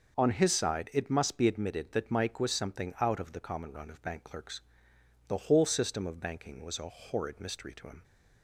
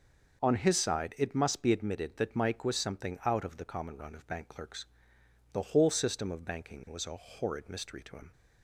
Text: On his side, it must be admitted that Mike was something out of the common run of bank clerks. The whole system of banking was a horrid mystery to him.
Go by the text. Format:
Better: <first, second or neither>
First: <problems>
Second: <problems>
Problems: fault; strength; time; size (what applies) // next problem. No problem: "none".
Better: neither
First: none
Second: none